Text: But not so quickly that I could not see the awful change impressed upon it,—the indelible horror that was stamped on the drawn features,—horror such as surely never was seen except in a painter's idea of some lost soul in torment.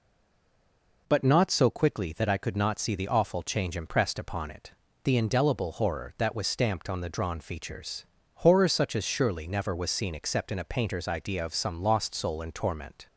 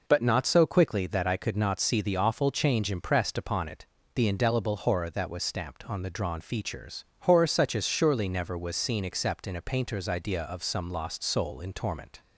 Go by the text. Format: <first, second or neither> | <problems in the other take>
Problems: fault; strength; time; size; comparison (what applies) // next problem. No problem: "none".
second | stays silent before the first word; until 1.0 s; 1.0 s long